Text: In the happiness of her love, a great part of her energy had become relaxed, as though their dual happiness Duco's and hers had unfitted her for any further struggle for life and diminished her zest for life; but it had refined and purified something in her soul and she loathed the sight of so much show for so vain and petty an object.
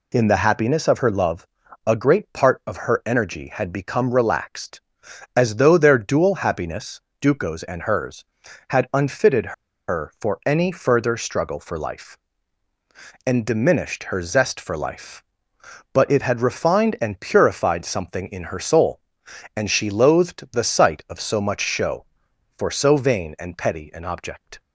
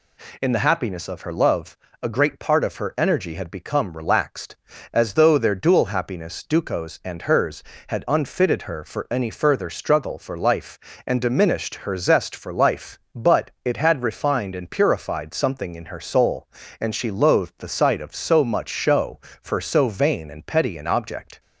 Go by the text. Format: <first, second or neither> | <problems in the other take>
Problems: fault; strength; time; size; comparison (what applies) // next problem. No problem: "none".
second | pauses between "happiness" and "Duco's"; slight; at 7.0 s; 0.18 s long // pauses between "unfitted" and "her"; slight; at 9.5 s; 0.36 s long